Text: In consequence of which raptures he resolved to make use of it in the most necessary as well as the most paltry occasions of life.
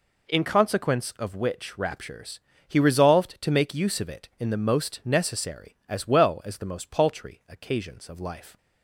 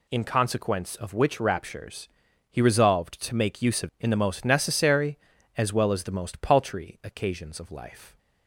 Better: first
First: pauses between "raptures" and "he"; slight; at 2.4 s; 0.26 s long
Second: pauses between "raptures" and "he"; at 2.0 s; 0.42 s long // skips "it"; at 3.9 s

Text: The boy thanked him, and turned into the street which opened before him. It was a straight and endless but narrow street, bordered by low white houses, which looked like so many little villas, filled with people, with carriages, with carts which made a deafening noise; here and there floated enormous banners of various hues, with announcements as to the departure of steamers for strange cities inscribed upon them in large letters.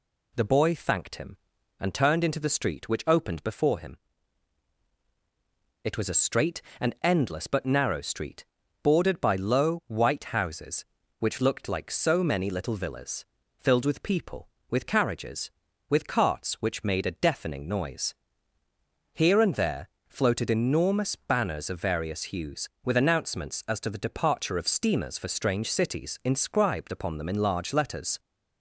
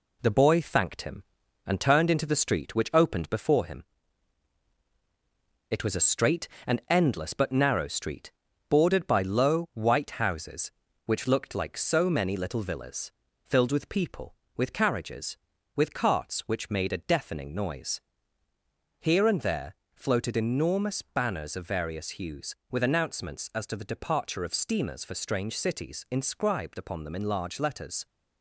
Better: first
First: pauses between "there" and "floated"; slight; at 19.8 s; 0.18 s long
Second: gets quieter; noticeable; throughout; 4.5 dB // pauses between "there" and "floated"; slight; at 19.7 s; 0.18 s long

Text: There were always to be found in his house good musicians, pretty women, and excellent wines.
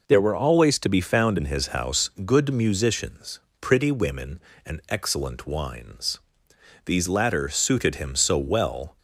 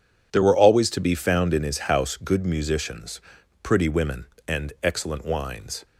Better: second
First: pauses between "house" and "good"; slight; at 2.0 s; 0.16 s long // goes on to say "These latter suited him so well"; strong; from 6.8 s on; 2.1 s long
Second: none

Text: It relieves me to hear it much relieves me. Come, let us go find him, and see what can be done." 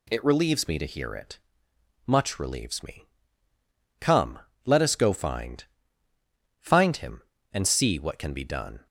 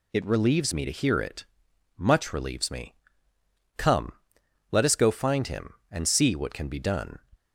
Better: second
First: pauses between "it" and "much"; noticeable; at 1.3 s; 0.72 s long // says "find" twice; at 6.6 s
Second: pauses between "it" and "much"; noticeable; at 1.4 s; 0.52 s long

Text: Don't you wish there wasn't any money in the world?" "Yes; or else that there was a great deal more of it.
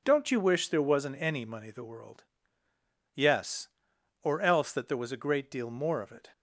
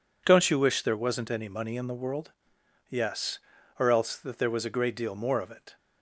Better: second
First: skips "in"; at 1.6 s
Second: none

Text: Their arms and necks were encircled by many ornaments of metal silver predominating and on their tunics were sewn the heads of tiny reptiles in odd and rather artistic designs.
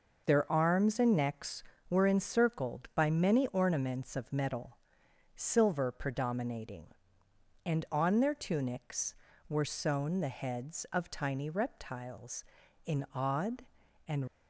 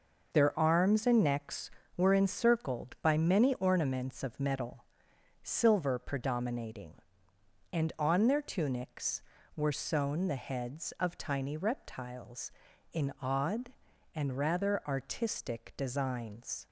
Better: second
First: pauses between "metal" and "silver"; noticeable; at 4.7 s; 0.58 s long // stops before "rather artistic designs"; at 14.2 s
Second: pauses between "metal" and "silver"; noticeable; at 4.8 s; 0.58 s long

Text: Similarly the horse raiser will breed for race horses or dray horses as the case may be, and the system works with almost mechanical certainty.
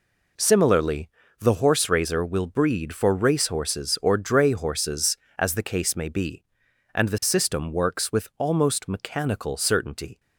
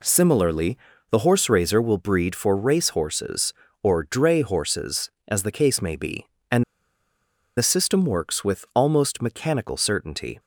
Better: first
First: pauses between "Similarly" and "the"; slight; at 1.0 s; 0.30 s long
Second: pauses between "Similarly" and "the"; slight; at 0.7 s; 0.34 s long // pauses between "and" and "the"; noticeable; at 6.6 s; 0.93 s long

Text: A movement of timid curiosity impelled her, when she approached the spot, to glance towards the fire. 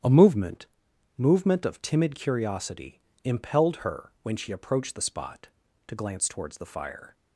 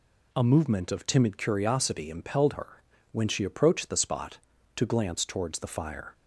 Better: second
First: starts louder than the rest; strong; until 1.5 s; 10 dB // says "movement" twice; at 1.1 s // pauses between "curiosity" and "impelled"; slight; at 3.0 s; 0.24 s long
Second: none

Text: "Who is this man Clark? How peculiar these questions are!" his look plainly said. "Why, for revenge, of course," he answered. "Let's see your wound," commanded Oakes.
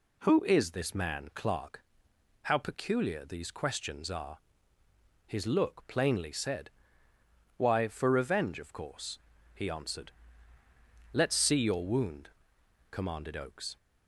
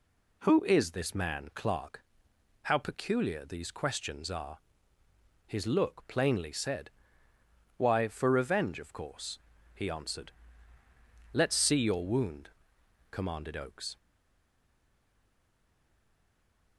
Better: first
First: none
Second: stays silent after the last word; strong; from 13.9 s on; 2.8 s long

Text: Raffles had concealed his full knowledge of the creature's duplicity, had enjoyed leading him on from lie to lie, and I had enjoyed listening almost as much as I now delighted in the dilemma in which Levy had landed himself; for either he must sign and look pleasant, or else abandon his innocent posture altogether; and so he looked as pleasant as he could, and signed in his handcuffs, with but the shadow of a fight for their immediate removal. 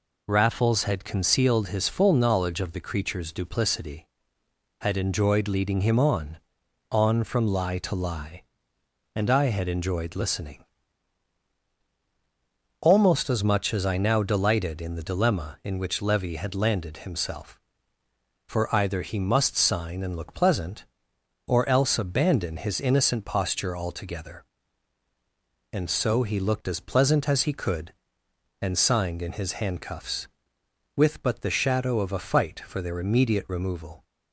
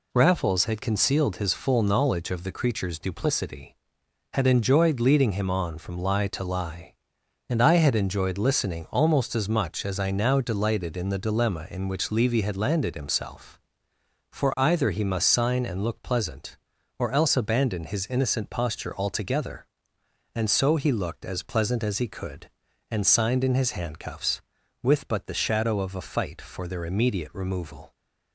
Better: second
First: says "on" twice; at 6.9 s // pauses between "listening" and "almost"; strong; at 10.6 s; 2.1 s long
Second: none

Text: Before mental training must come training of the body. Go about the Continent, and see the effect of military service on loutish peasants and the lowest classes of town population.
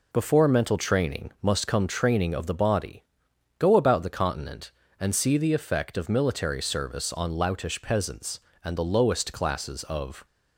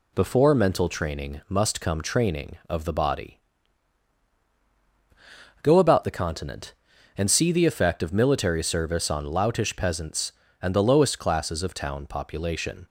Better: second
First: stops before "town population"; at 10.2 s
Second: none

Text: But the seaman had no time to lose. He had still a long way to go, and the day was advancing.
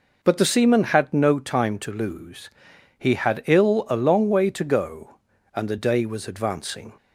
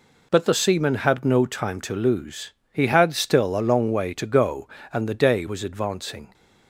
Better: second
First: says "ill" for "still"; at 3.4 s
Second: none

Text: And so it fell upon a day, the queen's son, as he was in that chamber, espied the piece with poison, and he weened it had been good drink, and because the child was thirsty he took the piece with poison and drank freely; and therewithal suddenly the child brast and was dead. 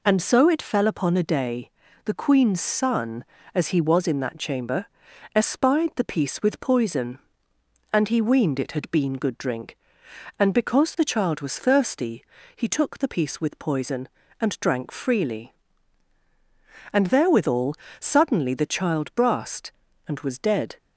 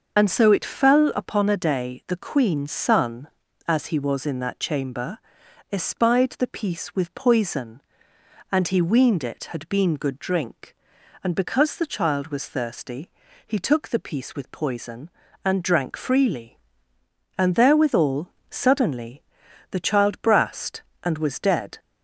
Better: first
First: pauses between "thirsty" and "he"; slight; at 12.2 s; 0.32 s long // pauses between "therewithal" and "suddenly"; slight; at 17.7 s; 0.24 s long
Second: loses the start of "And"; at 0.1 s; 40 ms // pauses between "thirsty" and "he"; slight; at 13.1 s; 0.34 s long // pauses between "therewithal" and "suddenly"; slight; at 18.2 s; 0.20 s long // pauses between "suddenly" and "the"; noticeable; at 19.2 s; 0.48 s long

